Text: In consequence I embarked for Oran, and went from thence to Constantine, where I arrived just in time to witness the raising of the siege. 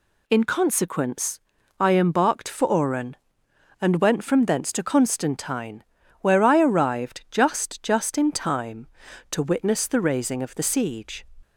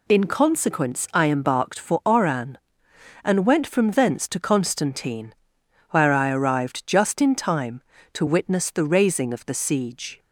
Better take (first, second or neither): second